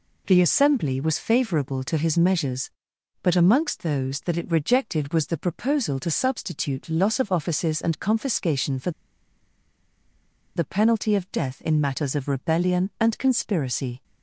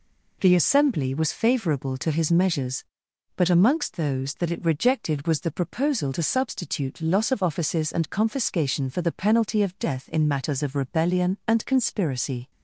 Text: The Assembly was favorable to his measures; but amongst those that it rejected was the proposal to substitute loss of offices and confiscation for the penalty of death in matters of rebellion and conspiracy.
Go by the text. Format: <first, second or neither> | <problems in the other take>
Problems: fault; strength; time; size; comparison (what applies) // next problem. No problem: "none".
second | pauses between "for" and "the"; strong; at 8.8 s; 1.6 s long